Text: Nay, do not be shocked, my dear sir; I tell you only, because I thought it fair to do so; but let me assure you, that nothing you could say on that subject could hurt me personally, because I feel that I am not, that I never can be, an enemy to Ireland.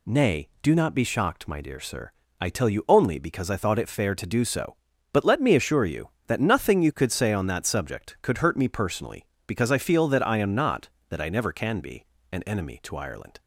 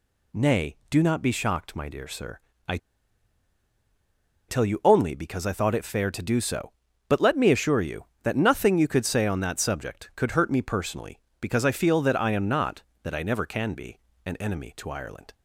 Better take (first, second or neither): first